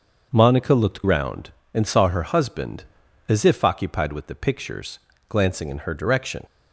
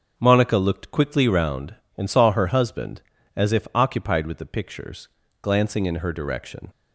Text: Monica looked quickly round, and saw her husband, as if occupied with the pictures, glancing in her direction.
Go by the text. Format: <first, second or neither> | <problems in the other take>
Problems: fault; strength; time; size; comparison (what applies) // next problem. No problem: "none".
second | starts louder than the rest; until 1.3 s; 6.5 dB; strong in the second // skips "quickly"; at 1.0 s